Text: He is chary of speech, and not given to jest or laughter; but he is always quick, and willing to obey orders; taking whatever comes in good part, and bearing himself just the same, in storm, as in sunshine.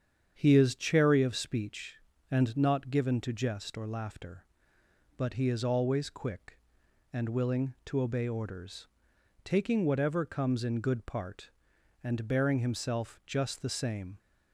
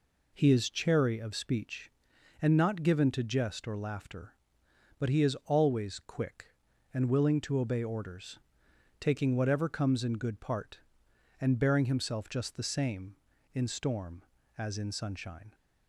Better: second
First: starts louder than the rest; strong; until 1.3 s; 8 dB // stops before "in storm as in sunshine"; at 14.1 s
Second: none

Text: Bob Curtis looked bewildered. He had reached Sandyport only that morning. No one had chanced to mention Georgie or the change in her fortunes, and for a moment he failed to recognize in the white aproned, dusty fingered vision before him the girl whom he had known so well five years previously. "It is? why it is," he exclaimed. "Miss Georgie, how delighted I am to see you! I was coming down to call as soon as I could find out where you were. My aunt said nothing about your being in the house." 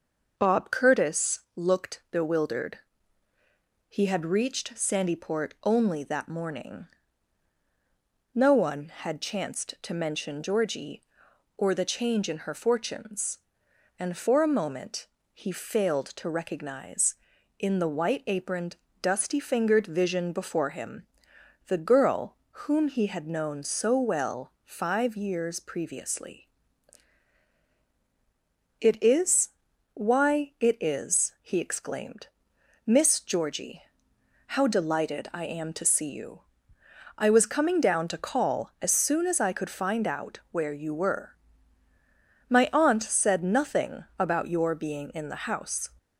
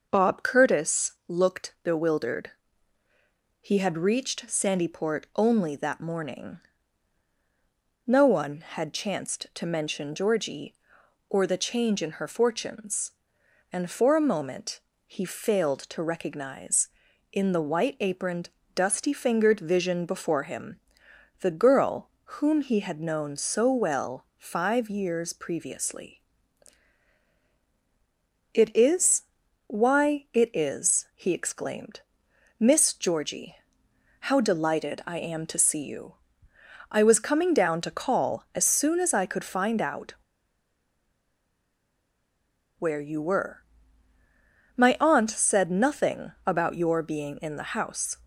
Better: first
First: pauses between "moment" and "he"; slight; at 15.0 s; 0.26 s long // pauses between "him" and "the"; noticeable; at 21.0 s; 0.62 s long // pauses between "girl" and "whom"; slight; at 22.3 s; 0.30 s long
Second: starts louder than the rest; noticeable; until 1.1 s; 6 dB // pauses between "moment" and "he"; slight; at 14.8 s; 0.26 s long // pauses between "him" and "the"; noticeable; at 20.7 s; 0.62 s long // pauses between "girl" and "whom"; slight; at 22.0 s; 0.30 s long // pauses between "out" and "where"; strong; at 40.1 s; 2.6 s long

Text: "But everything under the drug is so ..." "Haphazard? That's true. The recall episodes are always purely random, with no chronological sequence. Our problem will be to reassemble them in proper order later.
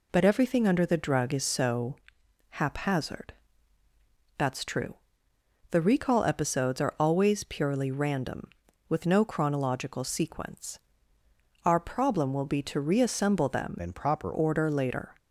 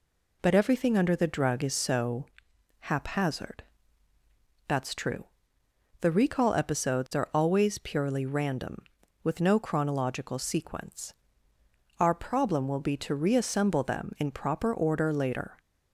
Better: second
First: changes voice from "in" to "proper"; from 13.7 to 14.3 s; 0.6 s long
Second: none

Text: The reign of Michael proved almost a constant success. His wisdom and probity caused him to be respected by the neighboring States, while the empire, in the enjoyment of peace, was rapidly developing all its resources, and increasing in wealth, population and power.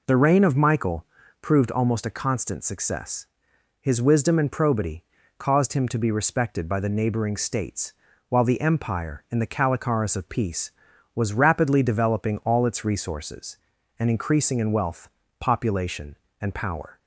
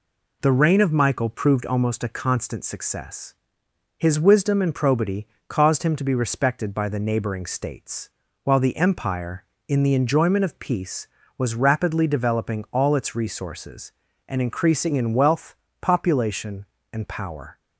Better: second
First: pauses between "Michael" and "proved"; slight; at 1.0 s; 0.36 s long // pauses between "probity" and "caused"; slight; at 5.0 s; 0.36 s long // says "calicaris" for "enjoyment"; at 9.4 s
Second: pauses between "probity" and "caused"; slight; at 5.2 s; 0.22 s long

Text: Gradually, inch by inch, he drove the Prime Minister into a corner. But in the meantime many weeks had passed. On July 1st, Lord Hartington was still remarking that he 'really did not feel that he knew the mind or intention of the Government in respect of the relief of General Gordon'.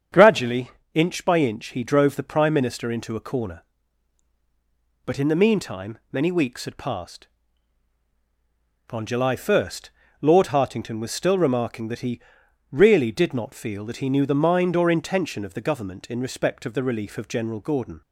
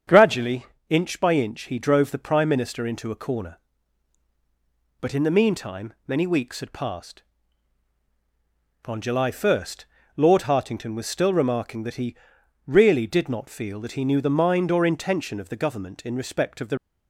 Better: first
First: starts louder than the rest; strong; until 1.3 s; 7.5 dB // pauses between "he" and "really"; noticeable; at 12.1 s; 0.50 s long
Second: starts louder than the rest; strong; until 1.3 s; 7.5 dB // pauses between "he" and "really"; noticeable; at 12.1 s; 0.50 s long // stops before "relief of General Gordon"; at 16.7 s

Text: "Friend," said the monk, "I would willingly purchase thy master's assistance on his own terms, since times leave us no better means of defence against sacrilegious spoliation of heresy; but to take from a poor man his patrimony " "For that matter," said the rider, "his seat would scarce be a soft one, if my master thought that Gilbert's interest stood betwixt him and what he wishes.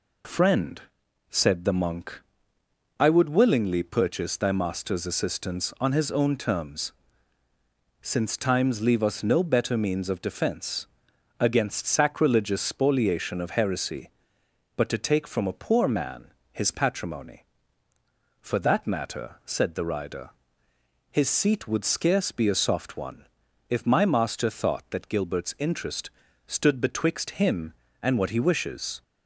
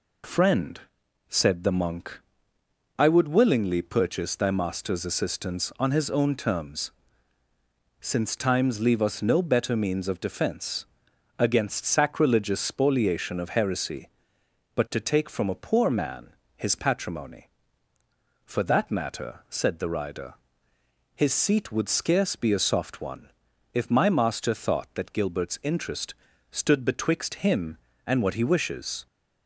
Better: neither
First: pauses between "defence" and "against"; noticeable; at 10.8 s; 0.50 s long // pauses between "man" and "his"; slight; at 16.3 s; 0.22 s long // pauses between "interest" and "stood"; slight; at 26.0 s; 0.36 s long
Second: pauses between "defence" and "against"; noticeable; at 10.8 s; 0.50 s long // pauses between "man" and "his"; slight; at 16.3 s; 0.24 s long // pauses between "interest" and "stood"; slight; at 26.1 s; 0.36 s long

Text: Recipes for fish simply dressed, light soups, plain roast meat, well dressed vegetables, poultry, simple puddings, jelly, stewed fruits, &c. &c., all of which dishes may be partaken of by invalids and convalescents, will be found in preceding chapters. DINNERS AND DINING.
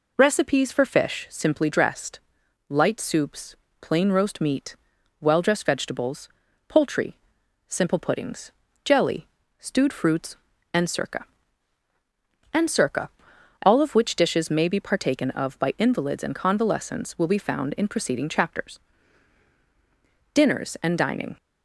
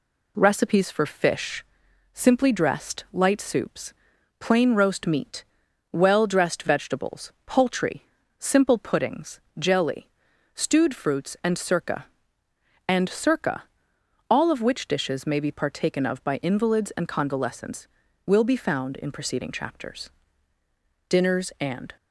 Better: first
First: none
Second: pauses between "fish" and "simply"; noticeable; at 1.6 s; 0.48 s long // stops before "DINING"; at 21.9 s

